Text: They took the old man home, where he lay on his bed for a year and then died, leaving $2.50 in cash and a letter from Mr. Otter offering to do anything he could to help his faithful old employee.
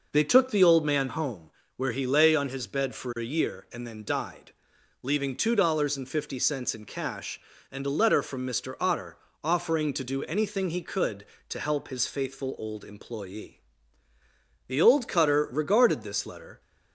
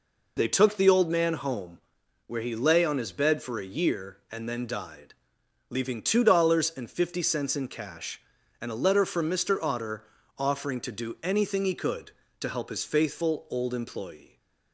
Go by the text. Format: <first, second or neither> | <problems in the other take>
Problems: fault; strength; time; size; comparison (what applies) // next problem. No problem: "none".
second | pauses between "Otter" and "offering"; slight; at 9.1 s; 0.26 s long; slight in the second // goes on to say "The old cutter regarded this letter"; strong; from 14.6 s on; 1.9 s long